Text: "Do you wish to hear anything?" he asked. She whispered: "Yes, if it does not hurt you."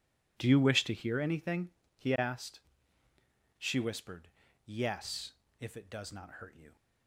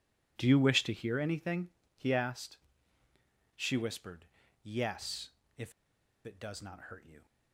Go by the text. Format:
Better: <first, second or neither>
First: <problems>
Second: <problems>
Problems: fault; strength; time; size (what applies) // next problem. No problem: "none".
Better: first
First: none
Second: pauses between "if" and "it"; noticeable; at 5.7 s; 0.52 s long